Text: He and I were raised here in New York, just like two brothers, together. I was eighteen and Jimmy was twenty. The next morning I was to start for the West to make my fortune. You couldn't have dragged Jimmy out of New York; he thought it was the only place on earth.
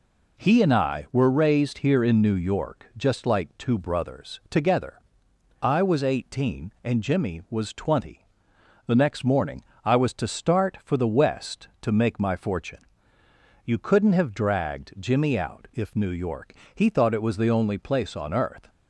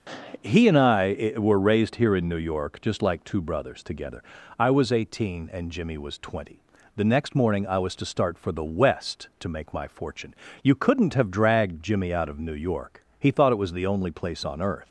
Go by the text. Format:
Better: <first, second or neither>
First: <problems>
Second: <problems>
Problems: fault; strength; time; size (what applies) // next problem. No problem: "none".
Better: second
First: pauses between "morning" and "I"; slight; at 9.6 s; 0.20 s long // says "if" for "of"; at 15.7 s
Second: none